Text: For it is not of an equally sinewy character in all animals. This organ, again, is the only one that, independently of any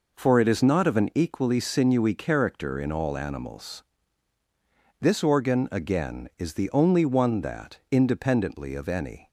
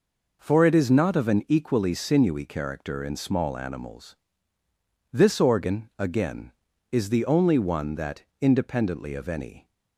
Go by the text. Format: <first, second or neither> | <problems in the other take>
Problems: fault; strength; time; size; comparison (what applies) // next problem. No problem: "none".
first | says "small" for "all"; at 3.1 s